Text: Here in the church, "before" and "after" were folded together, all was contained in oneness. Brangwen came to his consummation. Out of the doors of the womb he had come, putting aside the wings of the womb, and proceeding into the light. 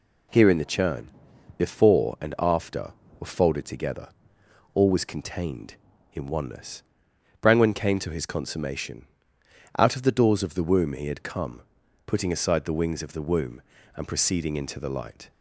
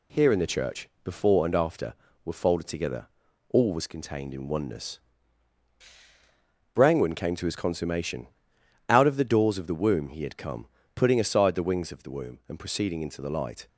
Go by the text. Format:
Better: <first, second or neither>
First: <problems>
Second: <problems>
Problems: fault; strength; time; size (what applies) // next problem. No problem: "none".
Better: second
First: says "churn" for "church"; at 0.6 s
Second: none